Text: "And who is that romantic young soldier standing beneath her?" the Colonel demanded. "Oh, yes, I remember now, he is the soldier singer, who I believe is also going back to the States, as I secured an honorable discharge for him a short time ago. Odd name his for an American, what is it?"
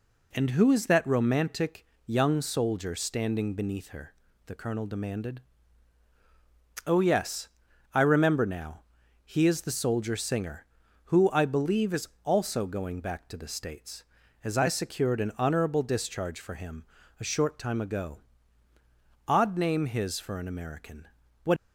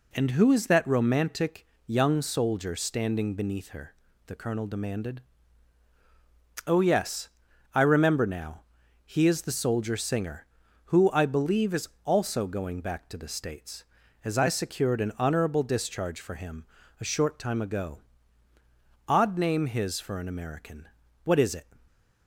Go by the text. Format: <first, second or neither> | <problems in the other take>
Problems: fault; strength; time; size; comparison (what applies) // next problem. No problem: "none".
second | pauses between "romantic" and "young"; slight; at 1.8 s; 0.20 s long; slight in the second // pauses between "is" and "also"; slight; at 12.0 s; 0.16 s long; slight in the second // pauses between "him" and "a"; slight; at 16.8 s; 0.34 s long; slight in the second // stops before "is it"; at 21.5 s